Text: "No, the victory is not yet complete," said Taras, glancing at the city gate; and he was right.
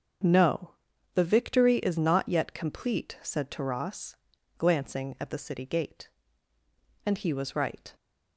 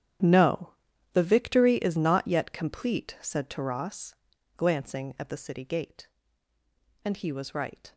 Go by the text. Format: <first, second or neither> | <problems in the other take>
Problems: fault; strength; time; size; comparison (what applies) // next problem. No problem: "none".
first | gets quieter; strong; throughout; 16 dB // starts louder than the rest; strong; until 1.6 s; 10 dB; also in the first